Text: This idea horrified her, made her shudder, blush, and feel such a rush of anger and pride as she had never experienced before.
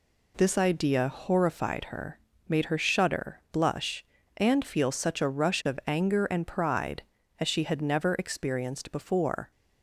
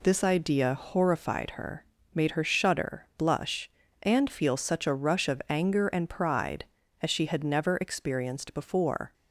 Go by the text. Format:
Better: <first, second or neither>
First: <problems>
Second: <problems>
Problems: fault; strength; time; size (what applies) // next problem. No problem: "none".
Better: neither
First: none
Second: none